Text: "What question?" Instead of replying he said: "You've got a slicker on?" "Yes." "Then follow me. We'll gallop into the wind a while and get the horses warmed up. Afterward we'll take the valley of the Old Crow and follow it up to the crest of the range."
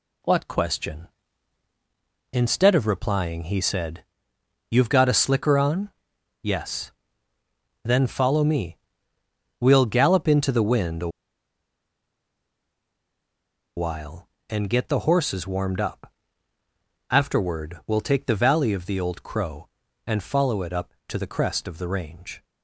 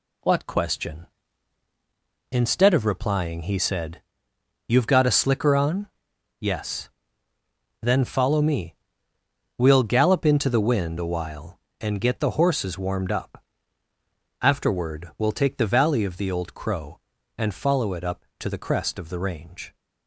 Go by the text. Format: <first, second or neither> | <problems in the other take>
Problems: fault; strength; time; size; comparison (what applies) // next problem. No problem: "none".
second | pauses between "a" and "while"; strong; at 11.0 s; 2.6 s long